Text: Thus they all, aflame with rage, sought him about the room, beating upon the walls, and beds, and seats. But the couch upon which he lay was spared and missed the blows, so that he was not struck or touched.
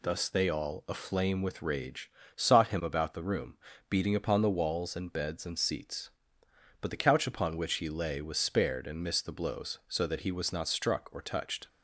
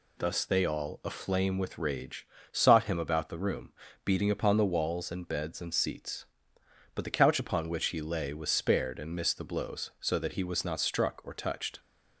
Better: neither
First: none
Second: none

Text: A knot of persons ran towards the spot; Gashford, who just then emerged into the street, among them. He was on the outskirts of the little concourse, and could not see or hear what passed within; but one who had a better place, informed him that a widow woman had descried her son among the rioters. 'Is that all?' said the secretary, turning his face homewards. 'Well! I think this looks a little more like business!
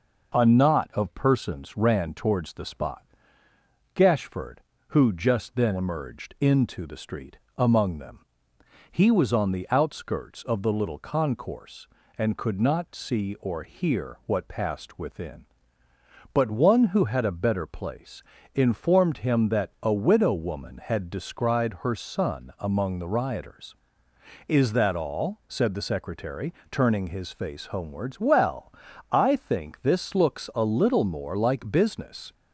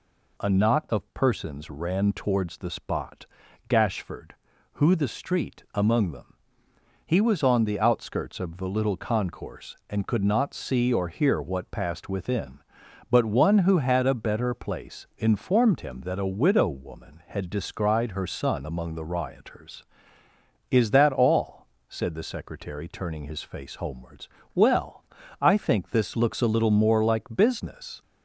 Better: first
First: none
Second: skips "just then emerged into"; at 4.9 s

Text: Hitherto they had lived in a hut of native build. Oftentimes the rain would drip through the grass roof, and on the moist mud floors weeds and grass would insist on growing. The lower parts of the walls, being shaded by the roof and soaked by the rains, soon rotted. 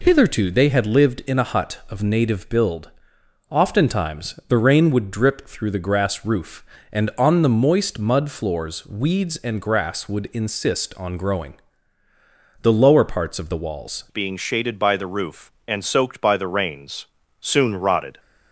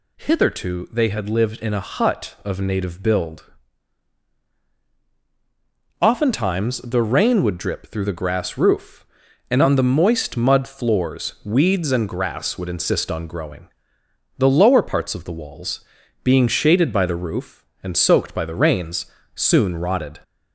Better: second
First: changes voice at "being"; from 14.0 s on; 4.1 s long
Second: none

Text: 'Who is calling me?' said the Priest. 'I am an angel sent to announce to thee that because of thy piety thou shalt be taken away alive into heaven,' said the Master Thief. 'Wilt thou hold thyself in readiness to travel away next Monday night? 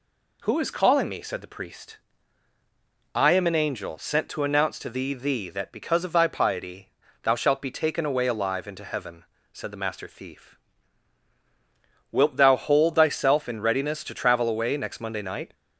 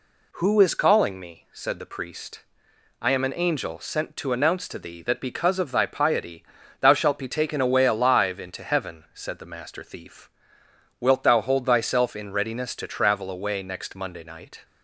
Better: second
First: says "thee" twice; at 5.1 s // pauses between "piety" and "thou"; slight; at 6.9 s; 0.32 s long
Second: pauses between "piety" and "thou"; at 6.4 s; 0.38 s long

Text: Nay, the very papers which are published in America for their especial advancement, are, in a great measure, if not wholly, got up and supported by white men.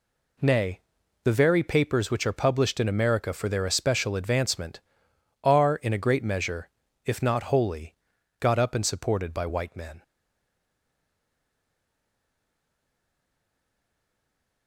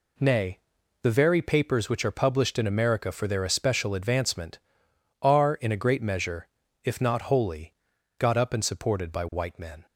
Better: second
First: stays silent after the last word; strong; from 10.0 s on; 4.6 s long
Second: none

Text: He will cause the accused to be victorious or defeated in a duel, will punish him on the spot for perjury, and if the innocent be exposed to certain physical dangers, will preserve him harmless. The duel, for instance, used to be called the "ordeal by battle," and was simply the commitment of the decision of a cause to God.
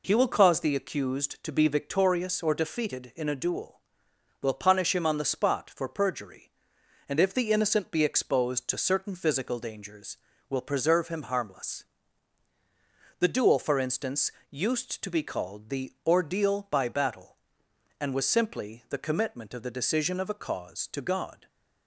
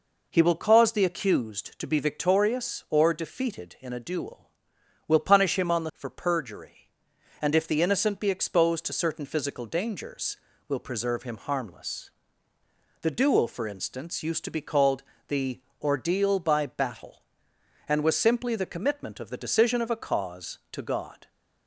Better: first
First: none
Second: skips "spot"; at 5.9 s // pauses between "called" and "the"; slight; at 15.0 s; 0.24 s long // pauses between "the" and "ordeal"; slight; at 15.5 s; 0.20 s long

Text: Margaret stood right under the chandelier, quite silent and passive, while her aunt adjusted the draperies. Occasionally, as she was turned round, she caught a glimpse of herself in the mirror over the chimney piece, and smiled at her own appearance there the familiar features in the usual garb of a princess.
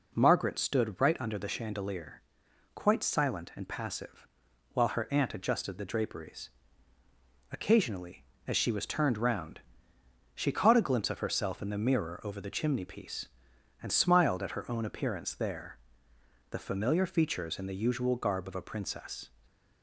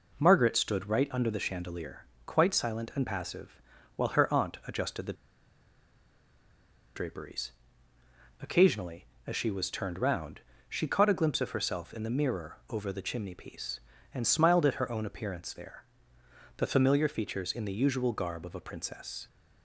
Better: first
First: pauses between "there" and "the"; noticeable; at 15.7 s; 0.72 s long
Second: pauses between "the" and "draperies"; strong; at 5.1 s; 1.8 s long // pauses between "there" and "the"; noticeable; at 15.8 s; 0.74 s long

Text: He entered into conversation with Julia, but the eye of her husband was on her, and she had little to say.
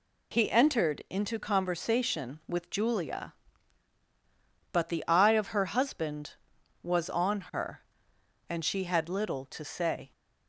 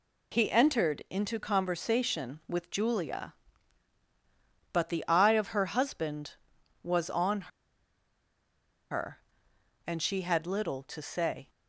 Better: first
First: none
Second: pauses between "on" and "her"; strong; at 7.5 s; 1.4 s long

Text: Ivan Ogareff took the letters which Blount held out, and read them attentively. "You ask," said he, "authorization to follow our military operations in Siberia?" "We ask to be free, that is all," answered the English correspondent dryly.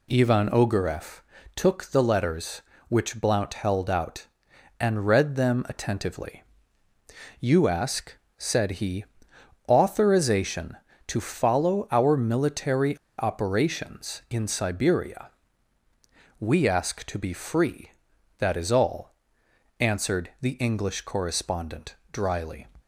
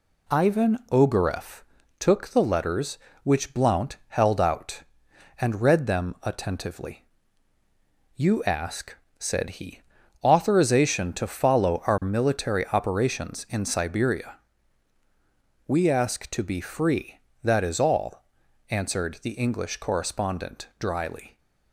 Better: second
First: pauses between "Ogareff" and "took"; slight; at 1.1 s; 0.36 s long // pauses between "military" and "operations"; slight; at 12.9 s; 0.20 s long // pauses between "correspondent" and "dryly"; slight; at 21.9 s; 0.16 s long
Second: pauses between "Ogareff" and "took"; at 1.6 s; 0.38 s long

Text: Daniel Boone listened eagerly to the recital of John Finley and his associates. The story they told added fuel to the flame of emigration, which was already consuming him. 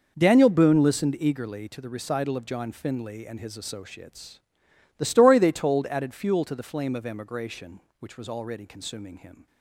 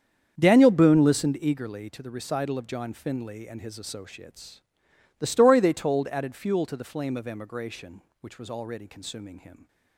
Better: first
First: none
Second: starts louder than the rest; strong; until 1.4 s; 7.5 dB

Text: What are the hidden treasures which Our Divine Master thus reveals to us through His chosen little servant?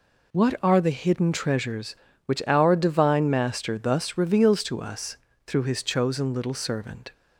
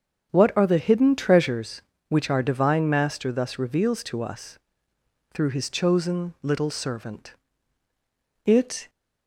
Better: first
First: pauses between "us" and "through"; slight; at 5.1 s; 0.30 s long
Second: starts louder than the rest; strong; until 1.3 s; 7.5 dB // pauses between "us" and "through"; noticeable; at 4.5 s; 0.74 s long // goes on to say "It"; slight; from 8.4 s on; 0.44 s long

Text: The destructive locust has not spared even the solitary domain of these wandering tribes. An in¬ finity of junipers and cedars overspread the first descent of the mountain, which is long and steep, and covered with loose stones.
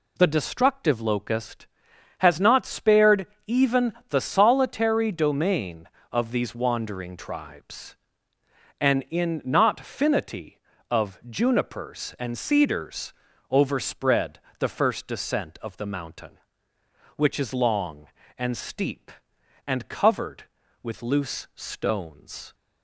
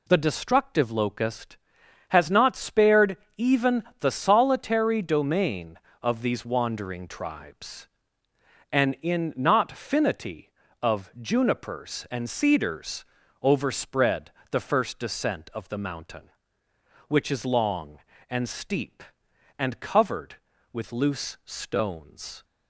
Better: neither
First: pauses between "spared" and "even"; slight; at 3.2 s; 0.18 s long // pauses between "even" and "the"; slight; at 3.9 s; 0.16 s long // pauses between "cedars" and "overspread"; at 13.1 s; 0.38 s long // pauses between "overspread" and "the"; slight; at 14.3 s; 0.20 s long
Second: pauses between "spared" and "even"; slight; at 3.1 s; 0.18 s long // pauses between "even" and "the"; slight; at 3.8 s; 0.16 s long // pauses between "cedars" and "overspread"; at 13.0 s; 0.38 s long // pauses between "overspread" and "the"; slight; at 14.3 s; 0.20 s long

